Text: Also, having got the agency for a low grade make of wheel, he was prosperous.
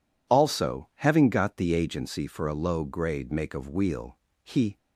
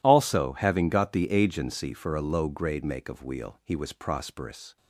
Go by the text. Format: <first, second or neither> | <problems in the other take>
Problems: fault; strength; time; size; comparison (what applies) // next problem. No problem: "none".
second | stops before "was prosperous"; at 4.7 s